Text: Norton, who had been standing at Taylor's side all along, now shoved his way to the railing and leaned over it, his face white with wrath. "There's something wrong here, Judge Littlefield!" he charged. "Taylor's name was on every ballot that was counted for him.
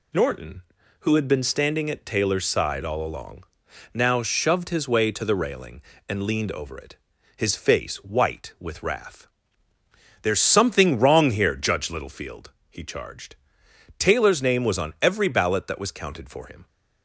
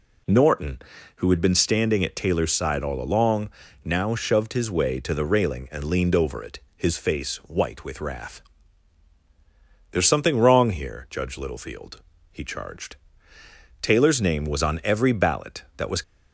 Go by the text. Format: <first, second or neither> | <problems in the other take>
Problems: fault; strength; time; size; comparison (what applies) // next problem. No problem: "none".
first | stops before "counted for him"; at 16.0 s